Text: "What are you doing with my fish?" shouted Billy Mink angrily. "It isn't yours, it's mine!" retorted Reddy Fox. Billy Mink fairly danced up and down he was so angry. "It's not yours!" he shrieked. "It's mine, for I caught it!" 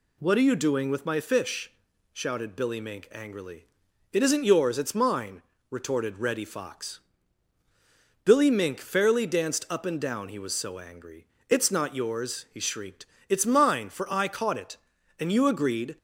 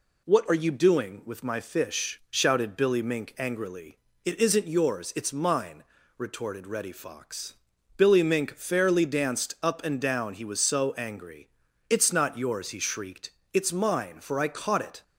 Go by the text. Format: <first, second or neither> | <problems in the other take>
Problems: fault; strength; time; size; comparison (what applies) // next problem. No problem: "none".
second | goes on to say "And you agreed"; noticeable; from 15.1 s on; 0.78 s long